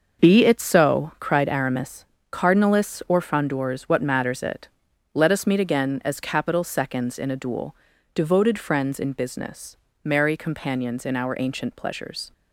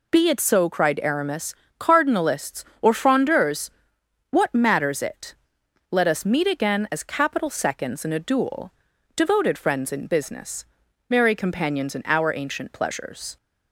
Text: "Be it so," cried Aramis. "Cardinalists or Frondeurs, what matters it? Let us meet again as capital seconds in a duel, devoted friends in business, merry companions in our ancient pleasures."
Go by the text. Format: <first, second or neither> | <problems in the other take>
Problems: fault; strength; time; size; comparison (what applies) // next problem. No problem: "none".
second | gets quieter; strong; throughout; 9.5 dB